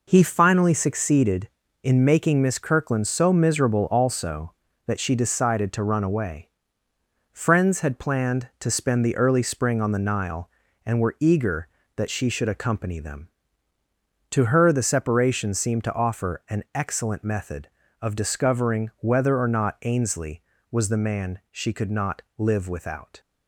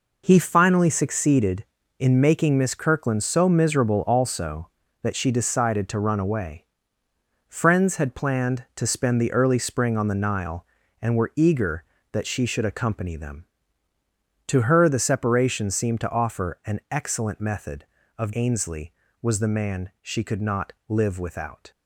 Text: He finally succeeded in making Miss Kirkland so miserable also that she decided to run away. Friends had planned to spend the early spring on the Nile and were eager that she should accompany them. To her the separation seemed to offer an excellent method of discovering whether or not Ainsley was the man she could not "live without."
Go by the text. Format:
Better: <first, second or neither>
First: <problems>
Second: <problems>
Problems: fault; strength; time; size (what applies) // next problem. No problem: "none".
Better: first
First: pauses between "not" and "live"; slight; at 22.2 s; 0.16 s long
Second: skips "discovering whether or not"; at 18.3 s // pauses between "not" and "live"; slight; at 20.7 s; 0.16 s long